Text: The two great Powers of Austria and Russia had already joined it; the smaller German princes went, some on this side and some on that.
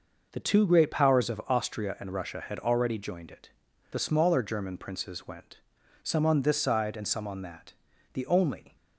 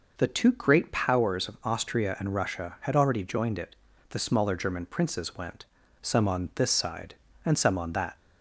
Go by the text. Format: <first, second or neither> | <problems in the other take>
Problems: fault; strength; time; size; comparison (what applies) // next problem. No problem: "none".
second | goes on to say "The only"; noticeable; from 8.1 s on; 0.62 s long